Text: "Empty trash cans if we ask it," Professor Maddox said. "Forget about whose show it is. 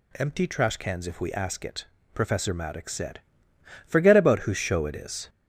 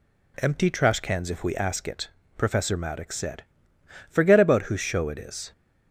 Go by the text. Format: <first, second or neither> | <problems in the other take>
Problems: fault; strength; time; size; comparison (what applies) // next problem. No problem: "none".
second | gets louder; noticeable; throughout; 5 dB